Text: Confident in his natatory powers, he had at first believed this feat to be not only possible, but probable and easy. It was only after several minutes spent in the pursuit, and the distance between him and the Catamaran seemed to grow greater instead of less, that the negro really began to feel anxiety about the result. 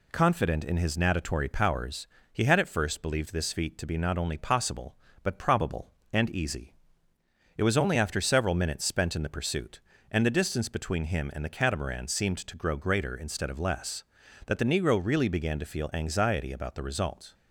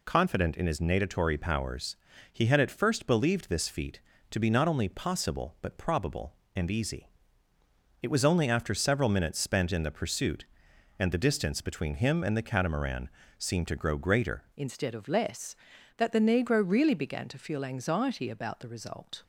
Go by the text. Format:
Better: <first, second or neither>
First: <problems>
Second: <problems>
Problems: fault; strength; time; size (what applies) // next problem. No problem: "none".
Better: first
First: none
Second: pauses between "Catamaran" and "seemed"; slight; at 13.0 s; 0.30 s long // changes voice at "instead"; from 14.5 s on; 4.7 s long